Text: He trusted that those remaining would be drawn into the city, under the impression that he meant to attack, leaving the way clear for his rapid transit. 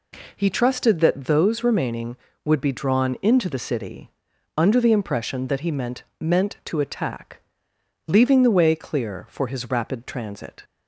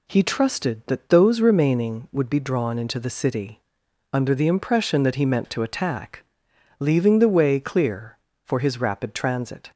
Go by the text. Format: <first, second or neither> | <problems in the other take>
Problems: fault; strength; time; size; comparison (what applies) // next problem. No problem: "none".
second | says "meant" twice; at 6.1 s